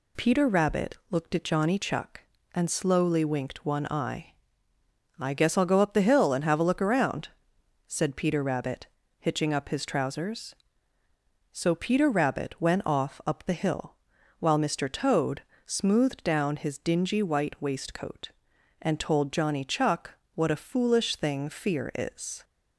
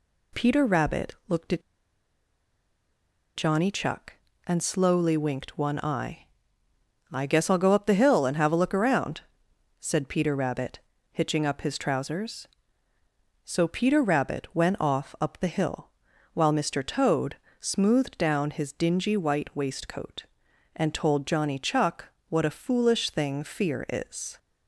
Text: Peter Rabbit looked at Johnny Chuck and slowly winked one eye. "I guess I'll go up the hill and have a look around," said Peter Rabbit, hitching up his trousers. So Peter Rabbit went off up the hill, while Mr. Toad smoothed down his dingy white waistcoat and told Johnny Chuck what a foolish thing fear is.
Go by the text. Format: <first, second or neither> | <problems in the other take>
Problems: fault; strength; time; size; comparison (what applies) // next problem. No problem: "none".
first | pauses between "at" and "Johnny"; strong; at 1.6 s; 1.7 s long // pauses between "Toad" and "smoothed"; slight; at 17.3 s; 0.24 s long; slight in the first // pauses between "Chuck" and "what"; slight; at 22.0 s; 0.24 s long; slight in the first